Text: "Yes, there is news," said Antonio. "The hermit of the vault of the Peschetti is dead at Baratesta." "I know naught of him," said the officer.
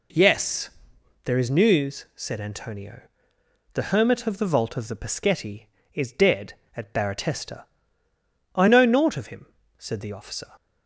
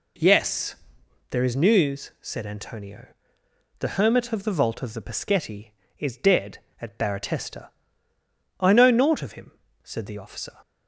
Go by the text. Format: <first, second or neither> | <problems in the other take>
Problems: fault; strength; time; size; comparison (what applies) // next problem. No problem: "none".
neither | none